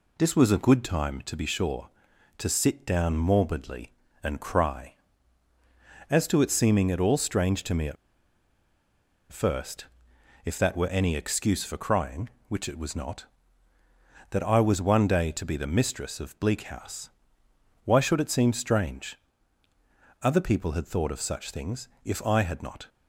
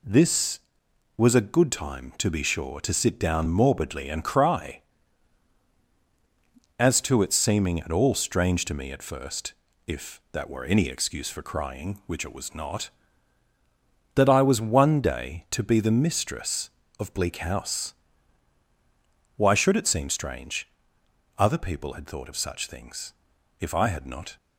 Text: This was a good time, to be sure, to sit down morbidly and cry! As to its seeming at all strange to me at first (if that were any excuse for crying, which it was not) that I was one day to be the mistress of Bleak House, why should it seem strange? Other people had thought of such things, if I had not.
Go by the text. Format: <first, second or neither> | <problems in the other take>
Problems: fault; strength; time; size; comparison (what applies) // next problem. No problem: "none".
second | pauses between "at" and "first"; strong; at 7.9 s; 1.3 s long